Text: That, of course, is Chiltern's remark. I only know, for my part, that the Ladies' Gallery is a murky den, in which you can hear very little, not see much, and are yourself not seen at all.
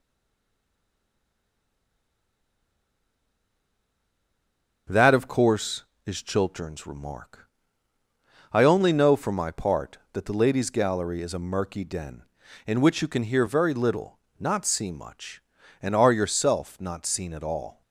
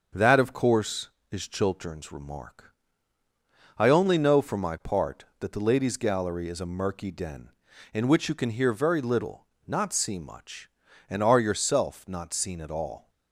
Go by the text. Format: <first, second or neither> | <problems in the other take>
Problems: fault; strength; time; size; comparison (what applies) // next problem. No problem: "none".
second | stays silent before the first word; strong; until 4.8 s; 4.8 s long // starts louder than the rest; until 6.1 s; 6.5 dB; also in the second